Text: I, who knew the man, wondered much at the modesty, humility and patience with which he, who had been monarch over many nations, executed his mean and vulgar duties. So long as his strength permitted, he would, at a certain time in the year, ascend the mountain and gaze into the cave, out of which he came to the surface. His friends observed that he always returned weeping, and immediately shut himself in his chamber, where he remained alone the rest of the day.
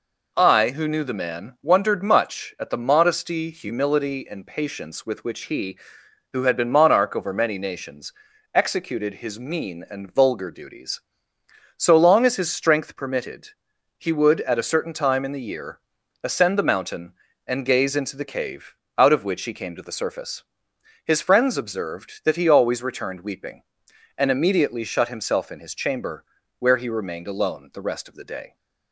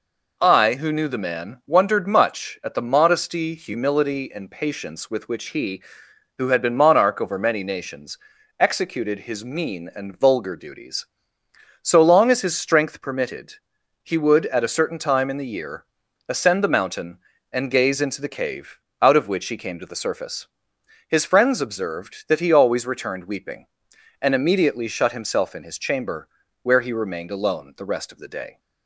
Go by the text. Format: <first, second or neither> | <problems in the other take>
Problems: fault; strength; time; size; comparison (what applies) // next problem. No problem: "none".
neither | none